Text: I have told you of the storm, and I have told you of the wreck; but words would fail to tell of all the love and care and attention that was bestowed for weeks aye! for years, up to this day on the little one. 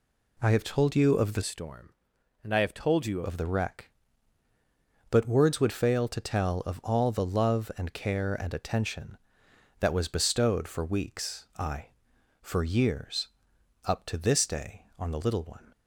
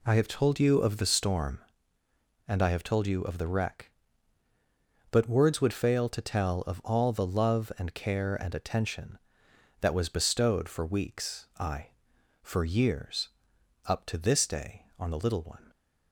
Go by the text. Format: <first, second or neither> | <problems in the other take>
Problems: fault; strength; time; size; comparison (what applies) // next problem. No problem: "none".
second | changes voice from "storm" to "you"; from 1.4 to 3.2 s; 1.8 s long